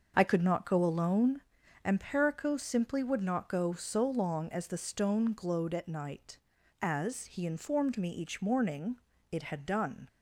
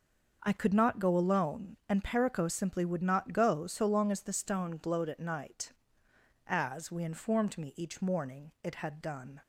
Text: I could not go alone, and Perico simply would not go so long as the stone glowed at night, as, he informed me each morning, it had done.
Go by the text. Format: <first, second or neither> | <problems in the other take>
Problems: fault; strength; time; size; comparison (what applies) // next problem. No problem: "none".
first | starts louder than the rest; until 1.4 s; 6.5 dB; also in the first // says "we" for "he"; at 6.8 s